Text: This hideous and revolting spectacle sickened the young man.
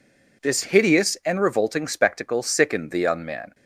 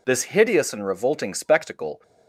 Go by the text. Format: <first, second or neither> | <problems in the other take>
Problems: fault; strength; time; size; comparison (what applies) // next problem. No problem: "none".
first | stops before "sickened the young man"; at 2.0 s